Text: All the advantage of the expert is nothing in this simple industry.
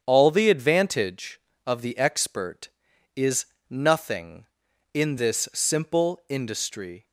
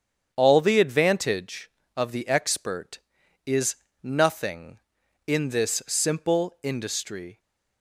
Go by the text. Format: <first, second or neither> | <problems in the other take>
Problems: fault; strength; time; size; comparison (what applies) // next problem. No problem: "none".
neither | starts louder than the rest; strong; the same in both // pauses between "is" and "nothing"; slight; the same in both